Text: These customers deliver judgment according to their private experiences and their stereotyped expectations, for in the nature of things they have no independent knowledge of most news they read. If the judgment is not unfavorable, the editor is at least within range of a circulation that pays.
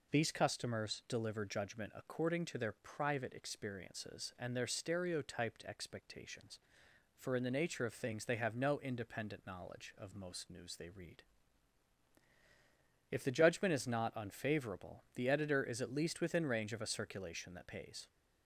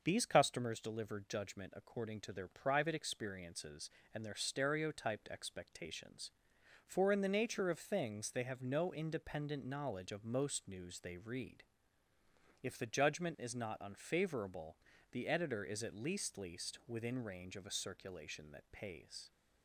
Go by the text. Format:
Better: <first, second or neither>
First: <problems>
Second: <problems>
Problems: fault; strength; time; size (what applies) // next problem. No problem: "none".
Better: first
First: none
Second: says "least" twice; at 16.3 s